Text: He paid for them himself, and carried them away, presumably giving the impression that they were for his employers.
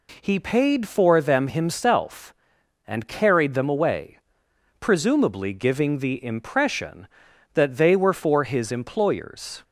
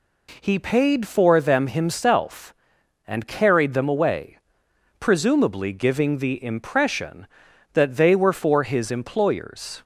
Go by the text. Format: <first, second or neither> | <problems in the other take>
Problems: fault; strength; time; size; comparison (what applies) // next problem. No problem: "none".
neither | none